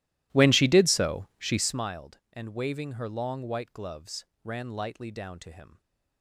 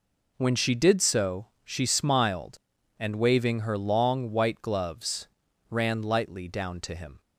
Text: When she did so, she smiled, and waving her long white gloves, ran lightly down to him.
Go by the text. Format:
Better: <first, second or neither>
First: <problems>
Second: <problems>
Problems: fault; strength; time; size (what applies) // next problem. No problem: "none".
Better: second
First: starts louder than the rest; strong; until 1.9 s; 16 dB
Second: none